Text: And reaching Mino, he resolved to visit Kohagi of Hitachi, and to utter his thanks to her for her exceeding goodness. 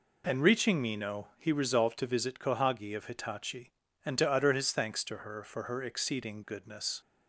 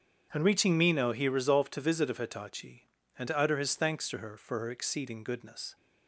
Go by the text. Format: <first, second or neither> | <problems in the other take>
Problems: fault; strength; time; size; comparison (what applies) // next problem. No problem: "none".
first | starts louder than the rest; strong; until 1.3 s; 7.5 dB // skips "Kohagi"; at 2.0 s